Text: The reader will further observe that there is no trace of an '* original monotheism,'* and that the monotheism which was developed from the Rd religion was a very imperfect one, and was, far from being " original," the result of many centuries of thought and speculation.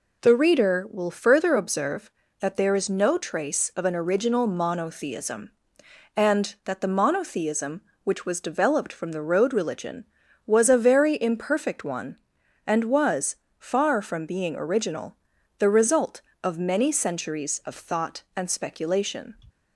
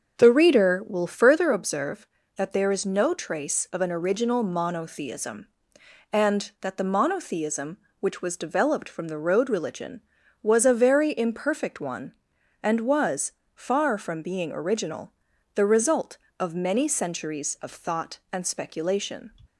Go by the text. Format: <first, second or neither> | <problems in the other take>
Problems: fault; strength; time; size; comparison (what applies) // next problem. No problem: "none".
first | starts louder than the rest; until 1.4 s; 6.5 dB